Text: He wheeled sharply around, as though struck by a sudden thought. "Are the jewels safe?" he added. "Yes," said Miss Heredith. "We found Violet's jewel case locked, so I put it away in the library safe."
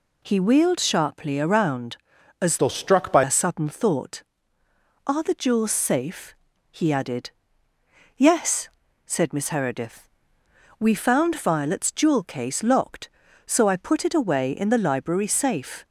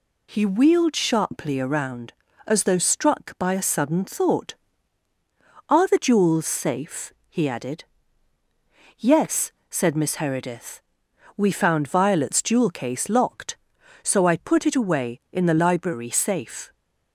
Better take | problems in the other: second | changes voice from "though" to "by"; from 2.5 to 3.2 s; 0.7 s long

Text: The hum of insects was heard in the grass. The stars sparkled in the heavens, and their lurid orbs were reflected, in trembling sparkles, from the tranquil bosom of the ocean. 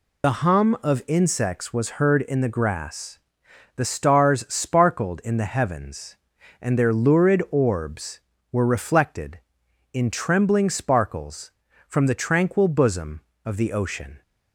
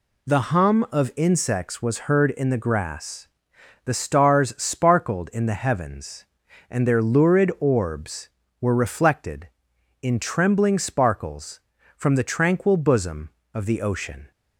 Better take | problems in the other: second | loses the start of "The"; at 0.2 s; 65 ms

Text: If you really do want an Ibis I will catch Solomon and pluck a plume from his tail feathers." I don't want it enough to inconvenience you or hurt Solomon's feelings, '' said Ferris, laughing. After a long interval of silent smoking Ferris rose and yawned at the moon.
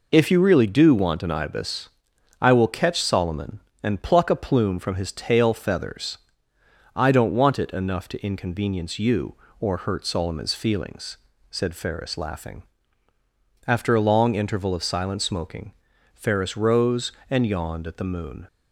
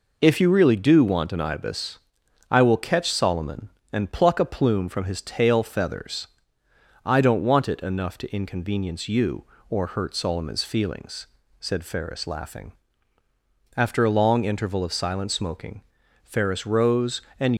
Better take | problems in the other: first | pauses between "Ibis" and "I"; noticeable; at 1.9 s; 0.52 s long; noticeable in the first // pauses between "smoking" and "Ferris"; at 15.8 s; 0.42 s long; also in the first // stops before "yawned at the moon"; at 17.5 s

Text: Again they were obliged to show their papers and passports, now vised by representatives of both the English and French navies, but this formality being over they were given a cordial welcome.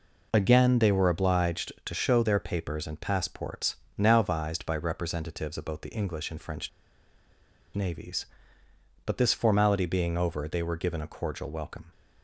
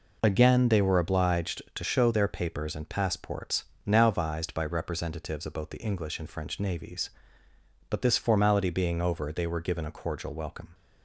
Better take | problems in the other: second | pauses between "French" and "navies"; at 6.6 s; 1.0 s long

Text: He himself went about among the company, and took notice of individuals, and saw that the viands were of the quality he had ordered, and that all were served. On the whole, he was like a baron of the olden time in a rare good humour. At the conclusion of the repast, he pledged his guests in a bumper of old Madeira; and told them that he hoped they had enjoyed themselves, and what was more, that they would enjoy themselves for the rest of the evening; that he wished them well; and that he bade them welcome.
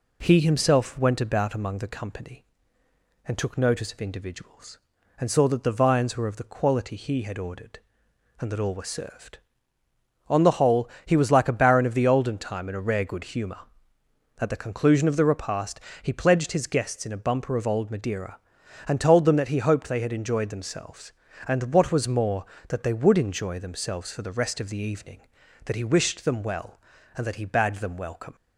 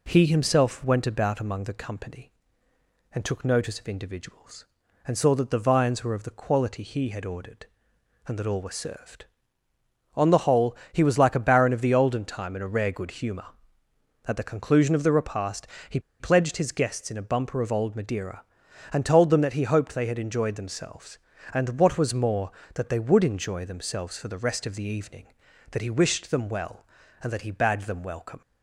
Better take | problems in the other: first | pauses between "he" and "pledged"; slight; at 15.9 s; 0.20 s long

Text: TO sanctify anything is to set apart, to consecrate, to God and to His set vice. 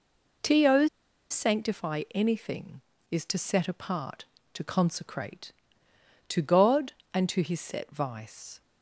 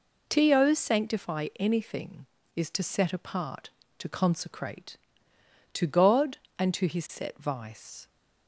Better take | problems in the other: second | pauses between "TO" and "sanctify"; at 0.8 s; 0.42 s long

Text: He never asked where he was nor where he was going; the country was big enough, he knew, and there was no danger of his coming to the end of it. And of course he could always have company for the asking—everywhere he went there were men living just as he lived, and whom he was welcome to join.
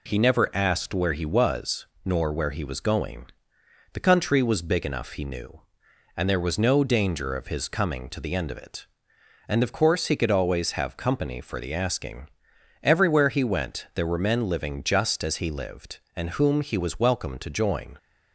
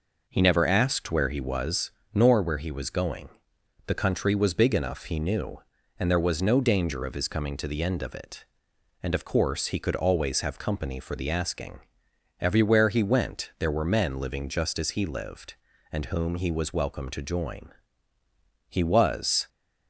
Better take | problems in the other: first | pauses between "was" and "nor"; slight; at 1.9 s; 0.24 s long; slight in the first // goes on to say "He was"; noticeable; from 18.6 s on; 0.80 s long

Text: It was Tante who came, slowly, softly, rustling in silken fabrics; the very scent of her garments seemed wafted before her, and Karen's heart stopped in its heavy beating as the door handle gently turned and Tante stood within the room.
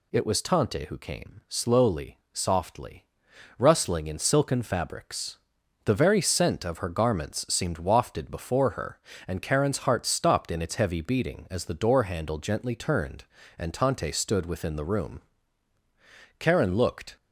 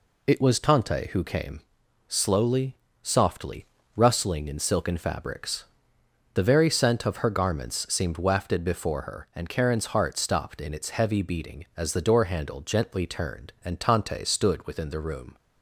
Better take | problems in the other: second | goes on to say "Karen looked"; noticeable; from 16.3 s on; 0.76 s long

